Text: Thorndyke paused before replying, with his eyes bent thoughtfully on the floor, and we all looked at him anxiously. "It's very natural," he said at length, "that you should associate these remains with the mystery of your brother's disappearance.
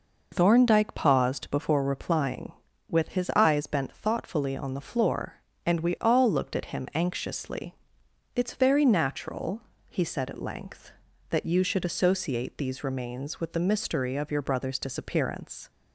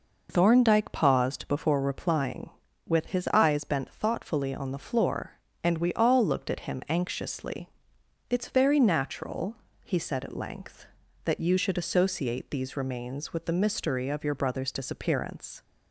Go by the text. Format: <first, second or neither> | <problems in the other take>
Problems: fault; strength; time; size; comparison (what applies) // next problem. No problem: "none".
neither | none